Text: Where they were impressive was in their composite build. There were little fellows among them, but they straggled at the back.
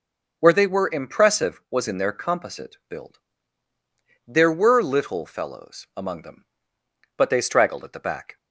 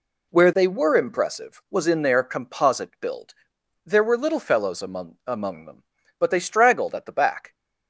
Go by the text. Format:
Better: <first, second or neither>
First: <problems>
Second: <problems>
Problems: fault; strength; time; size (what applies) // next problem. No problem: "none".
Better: first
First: none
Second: says "among" twice; at 5.2 s